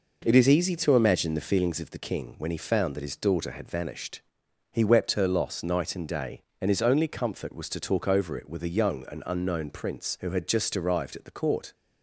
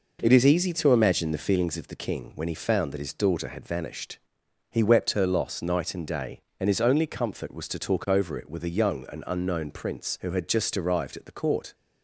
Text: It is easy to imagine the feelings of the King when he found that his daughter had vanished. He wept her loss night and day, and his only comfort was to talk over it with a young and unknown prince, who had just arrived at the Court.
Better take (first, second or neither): neither